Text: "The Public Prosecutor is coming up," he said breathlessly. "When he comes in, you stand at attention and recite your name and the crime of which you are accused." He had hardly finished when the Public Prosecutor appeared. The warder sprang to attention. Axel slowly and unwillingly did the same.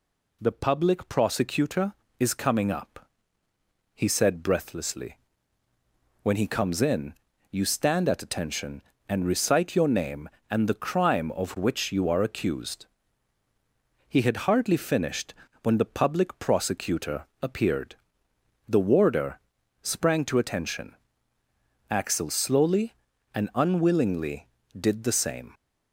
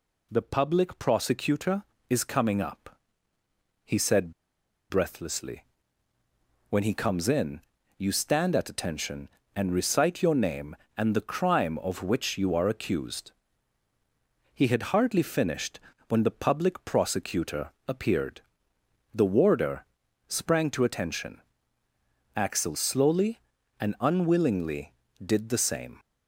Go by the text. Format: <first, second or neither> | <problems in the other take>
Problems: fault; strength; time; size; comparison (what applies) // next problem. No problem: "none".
first | pauses between "said" and "breathlessly"; noticeable; at 4.3 s; 0.59 s long // pauses between "finished" and "when"; slight; at 15.7 s; 0.28 s long; slight in the first // pauses between "Prosecutor" and "appeared"; slight; at 17.7 s; 0.16 s long; slight in the first // pauses between "warder" and "sprang"; at 19.8 s; 0.42 s long; also in the first